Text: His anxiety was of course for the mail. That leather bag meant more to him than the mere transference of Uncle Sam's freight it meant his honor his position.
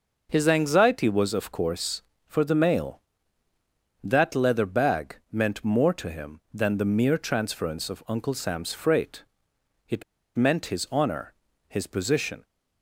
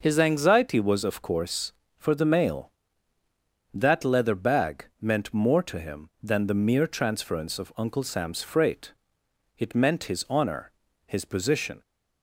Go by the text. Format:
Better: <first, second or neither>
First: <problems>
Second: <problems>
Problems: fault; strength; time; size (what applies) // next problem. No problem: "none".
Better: second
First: pauses between "bag" and "meant"; slight; at 5.1 s; 0.16 s long // pauses between "freight" and "it"; noticeable; at 9.2 s; 0.64 s long // pauses between "it" and "meant"; slight; at 10.0 s; 0.33 s long // pauses between "honor" and "his"; slight; at 11.3 s; 0.34 s long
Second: pauses between "bag" and "meant"; slight; at 4.8 s; 0.16 s long // pauses between "freight" and "it"; noticeable; at 8.9 s; 0.64 s long // pauses between "honor" and "his"; slight; at 10.7 s; 0.34 s long